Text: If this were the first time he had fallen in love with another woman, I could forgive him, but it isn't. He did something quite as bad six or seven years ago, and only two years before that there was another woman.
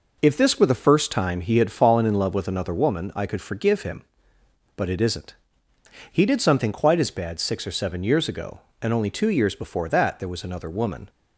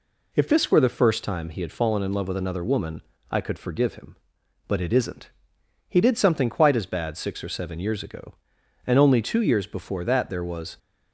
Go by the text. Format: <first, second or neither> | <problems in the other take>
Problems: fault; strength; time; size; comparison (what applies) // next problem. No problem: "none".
first | stops before "another woman"; at 10.7 s